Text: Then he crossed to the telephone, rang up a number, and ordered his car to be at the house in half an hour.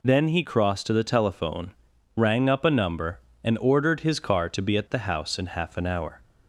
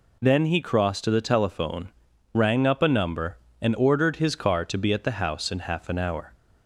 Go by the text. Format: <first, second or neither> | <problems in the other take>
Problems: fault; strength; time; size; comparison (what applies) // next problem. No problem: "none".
neither | none